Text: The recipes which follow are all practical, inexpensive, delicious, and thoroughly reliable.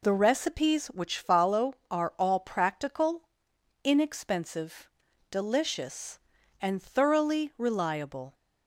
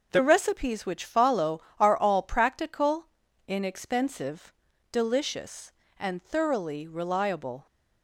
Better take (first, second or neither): neither